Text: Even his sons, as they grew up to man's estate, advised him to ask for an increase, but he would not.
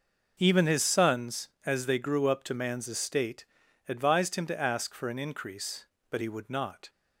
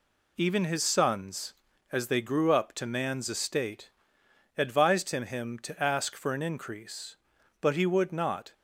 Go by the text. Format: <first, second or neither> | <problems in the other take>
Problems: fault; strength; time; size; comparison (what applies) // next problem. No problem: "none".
first | says "him" twice; at 5.2 s